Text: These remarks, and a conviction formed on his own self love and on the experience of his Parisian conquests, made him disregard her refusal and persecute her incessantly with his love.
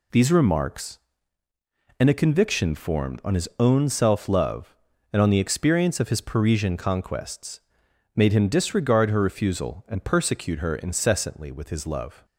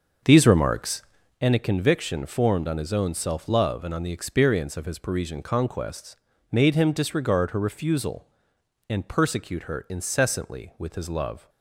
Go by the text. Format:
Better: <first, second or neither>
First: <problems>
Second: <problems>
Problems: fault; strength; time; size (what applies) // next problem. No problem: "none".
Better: first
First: none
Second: starts louder than the rest; until 1.5 s; 6.5 dB